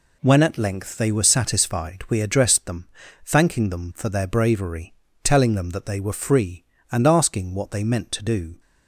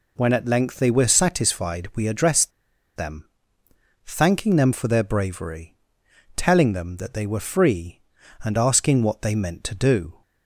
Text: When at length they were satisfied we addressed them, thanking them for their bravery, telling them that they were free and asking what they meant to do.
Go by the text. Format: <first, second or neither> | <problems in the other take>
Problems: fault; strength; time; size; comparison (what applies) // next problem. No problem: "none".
first | pauses between "addressed" and "them"; at 2.5 s; 0.45 s long